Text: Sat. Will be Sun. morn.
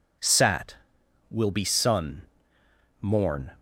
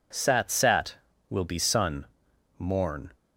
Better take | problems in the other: first | says "Sat" twice; at 0.5 s

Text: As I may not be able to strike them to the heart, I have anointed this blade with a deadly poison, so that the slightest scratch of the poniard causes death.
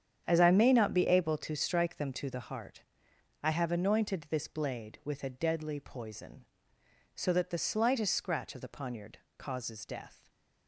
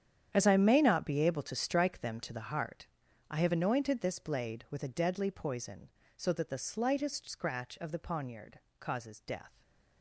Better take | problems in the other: first | gets quieter; strong; throughout; 15.5 dB // starts louder than the rest; strong; until 1.3 s; 9 dB; strong in the first // pauses between "poniard" and "causes"; slight; at 8.5 s; 0.22 s long; slight in the first // stays silent after the last word; slight; from 9.4 s on; 0.6 s long; slight in the first

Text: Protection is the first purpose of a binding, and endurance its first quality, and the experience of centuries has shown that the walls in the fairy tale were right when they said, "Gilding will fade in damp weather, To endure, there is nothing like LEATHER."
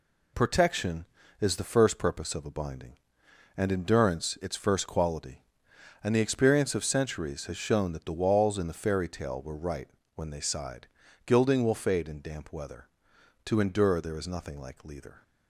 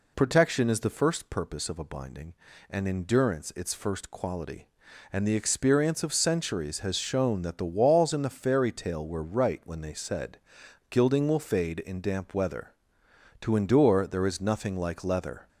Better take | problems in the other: second | pauses between "right" and "when"; slight; at 9.8 s; 0.26 s long // says "sighed" for "said"; at 10.4 s

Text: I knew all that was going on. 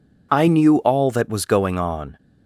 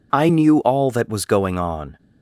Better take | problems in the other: neither | none

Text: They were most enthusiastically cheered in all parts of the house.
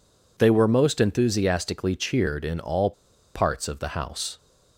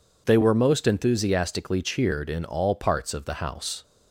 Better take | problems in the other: second | pauses between "all" and "parts"; at 2.9 s; 0.42 s long

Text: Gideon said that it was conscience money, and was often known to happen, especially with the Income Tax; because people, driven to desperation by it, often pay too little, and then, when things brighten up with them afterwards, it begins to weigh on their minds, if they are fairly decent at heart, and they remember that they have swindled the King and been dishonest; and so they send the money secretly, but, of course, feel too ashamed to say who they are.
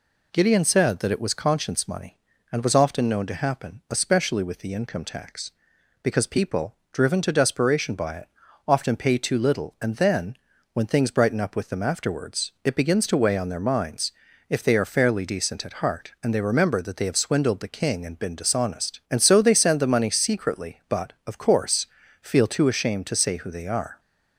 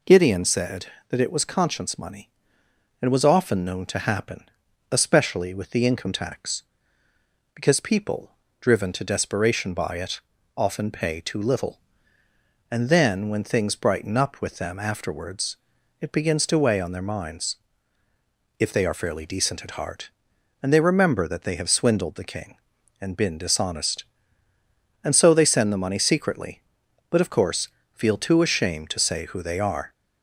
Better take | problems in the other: neither | none

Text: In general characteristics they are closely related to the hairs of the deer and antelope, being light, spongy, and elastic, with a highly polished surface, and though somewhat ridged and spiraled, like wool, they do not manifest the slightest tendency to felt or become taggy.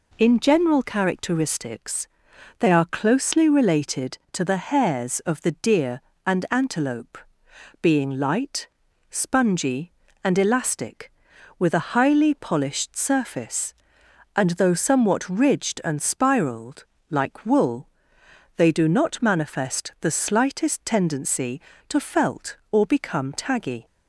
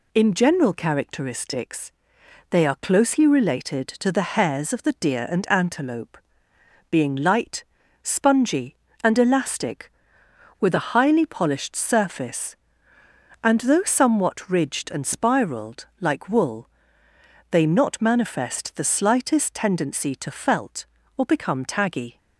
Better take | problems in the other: first | pauses between "characteristics" and "they"; noticeable; at 1.9 s; 0.58 s long; noticeable in the first // skips "do"; at 17.6 s

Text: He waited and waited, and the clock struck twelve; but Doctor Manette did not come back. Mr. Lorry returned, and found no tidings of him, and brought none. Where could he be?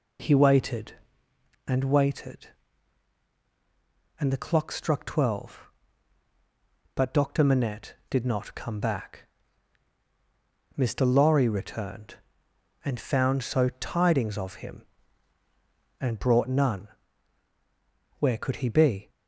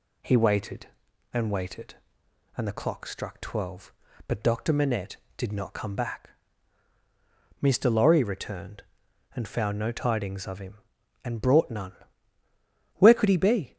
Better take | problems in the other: second | says "so" for "no"; at 13.4 s

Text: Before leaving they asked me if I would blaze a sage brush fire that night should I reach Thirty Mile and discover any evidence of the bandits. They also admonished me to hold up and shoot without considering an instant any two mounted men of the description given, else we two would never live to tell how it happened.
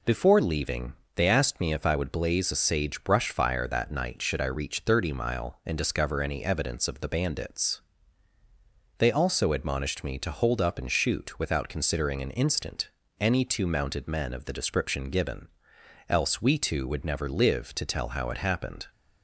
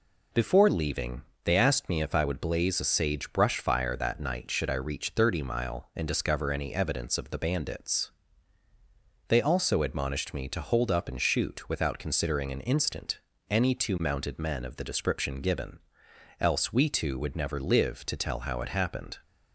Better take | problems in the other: neither | pauses between "leaving" and "they"; slight; the same in both // pauses between "instant" and "any"; slight; the same in both

